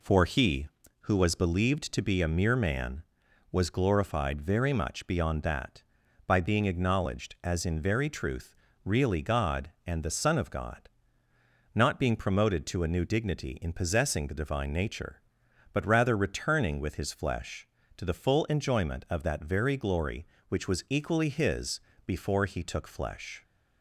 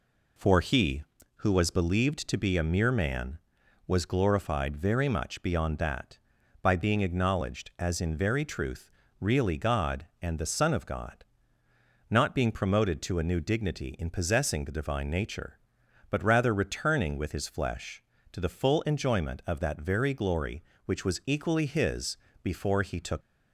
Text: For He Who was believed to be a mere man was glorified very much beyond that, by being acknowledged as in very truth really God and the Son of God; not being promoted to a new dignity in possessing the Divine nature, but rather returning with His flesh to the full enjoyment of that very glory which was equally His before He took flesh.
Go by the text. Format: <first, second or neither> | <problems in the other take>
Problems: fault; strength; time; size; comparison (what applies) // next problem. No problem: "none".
first | pauses between "truth" and "really"; slight; at 8.9 s; 0.28 s long; slight in the first // pauses between "His" and "before"; slight; at 22.1 s; 0.26 s long; slight in the first // stops before "flesh"; at 23.2 s